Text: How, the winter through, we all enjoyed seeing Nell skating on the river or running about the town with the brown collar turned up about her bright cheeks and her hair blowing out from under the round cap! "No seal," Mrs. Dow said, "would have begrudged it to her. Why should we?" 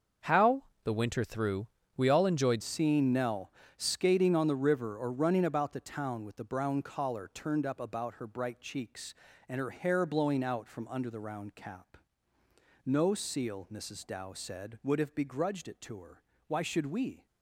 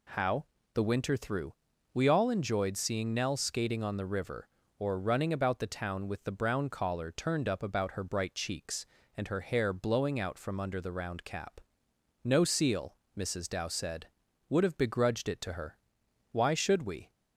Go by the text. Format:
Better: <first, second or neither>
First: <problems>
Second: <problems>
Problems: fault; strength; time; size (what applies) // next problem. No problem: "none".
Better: second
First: starts louder than the rest; until 1.4 s; 6 dB // changes voice at "seeing"; from 2.6 s on; 14.6 s long // pauses between "Nell" and "skating"; slight; at 3.5 s; 0.26 s long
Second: none